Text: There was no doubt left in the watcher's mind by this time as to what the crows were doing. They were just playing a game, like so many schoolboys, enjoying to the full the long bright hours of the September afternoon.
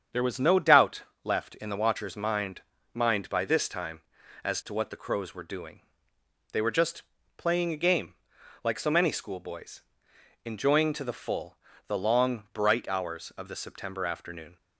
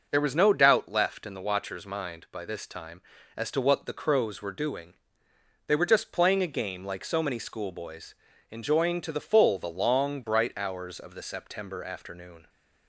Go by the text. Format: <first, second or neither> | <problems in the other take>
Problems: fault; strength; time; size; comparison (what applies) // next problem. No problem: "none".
second | starts louder than the rest; strong; until 1.3 s; 7.5 dB // pauses between "doubt" and "left"; slight; at 1.0 s; 0.20 s long // says "mind" twice; at 2.9 s // pauses between "just" and "playing"; slight; at 7.0 s; 0.34 s long // pauses between "full" and "the"; slight; at 11.5 s; 0.32 s long